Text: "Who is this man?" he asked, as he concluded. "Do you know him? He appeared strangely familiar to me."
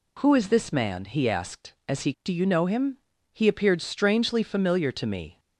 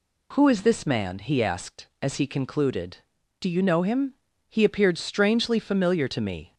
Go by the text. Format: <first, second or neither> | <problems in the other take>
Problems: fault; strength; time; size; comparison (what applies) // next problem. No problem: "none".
second | skips "concluded"; at 2.1 s